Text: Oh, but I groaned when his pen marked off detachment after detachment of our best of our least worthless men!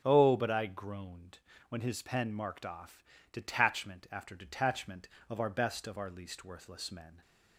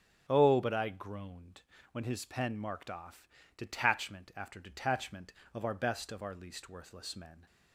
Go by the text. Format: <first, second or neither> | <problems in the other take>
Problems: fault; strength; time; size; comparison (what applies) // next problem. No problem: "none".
neither | starts louder than the rest; strong; the same in both // pauses between "groaned" and "when"; slight; the same in both // pauses between "off" and "detachment"; slight; the same in both